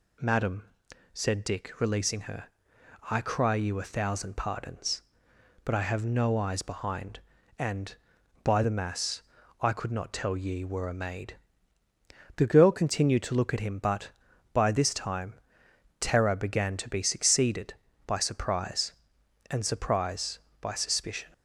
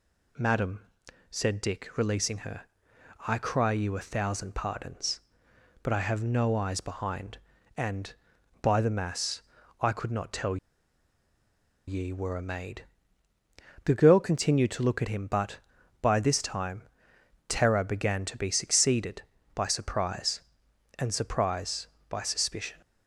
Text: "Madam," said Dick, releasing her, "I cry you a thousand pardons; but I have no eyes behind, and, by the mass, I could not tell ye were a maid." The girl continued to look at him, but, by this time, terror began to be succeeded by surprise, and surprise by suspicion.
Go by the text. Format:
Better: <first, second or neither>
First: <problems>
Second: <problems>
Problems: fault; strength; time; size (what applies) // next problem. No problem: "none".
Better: first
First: none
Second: pauses between "tell" and "ye"; strong; at 10.5 s; 1.3 s long